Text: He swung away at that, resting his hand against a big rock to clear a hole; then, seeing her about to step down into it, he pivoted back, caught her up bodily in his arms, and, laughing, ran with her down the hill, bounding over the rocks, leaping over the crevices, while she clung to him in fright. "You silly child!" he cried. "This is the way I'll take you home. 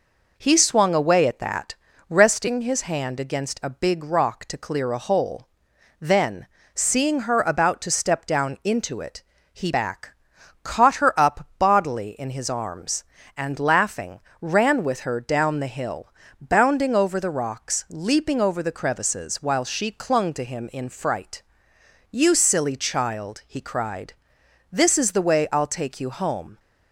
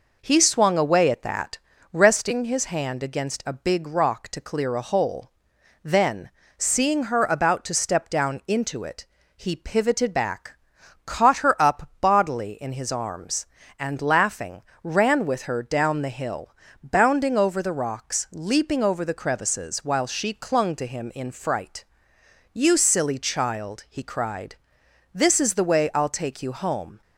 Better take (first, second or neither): second